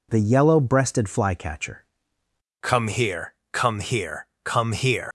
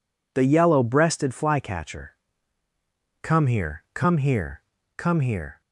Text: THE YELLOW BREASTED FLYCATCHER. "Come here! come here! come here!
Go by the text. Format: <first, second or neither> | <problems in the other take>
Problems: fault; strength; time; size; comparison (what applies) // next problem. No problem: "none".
second | leaves "here" unfinished; at 5.0 s; 85 ms